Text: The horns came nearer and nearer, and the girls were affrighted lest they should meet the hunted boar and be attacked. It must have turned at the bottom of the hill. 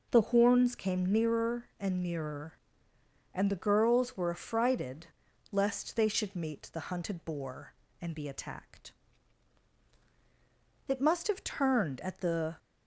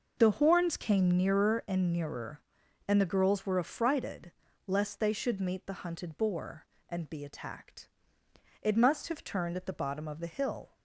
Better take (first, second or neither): second